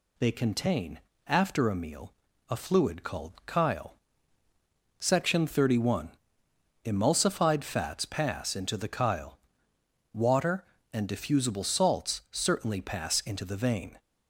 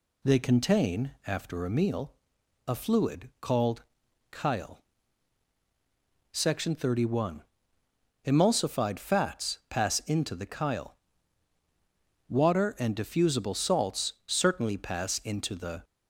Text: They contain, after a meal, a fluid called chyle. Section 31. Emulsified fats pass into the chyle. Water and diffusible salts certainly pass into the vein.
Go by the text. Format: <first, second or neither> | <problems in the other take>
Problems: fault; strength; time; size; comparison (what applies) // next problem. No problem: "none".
first | pauses between "called" and "chyle"; noticeable; at 3.8 s; 0.48 s long; slight in the first // pauses between "salts" and "certainly"; slight; at 14.1 s; 0.16 s long // stops before "vein"; at 15.8 s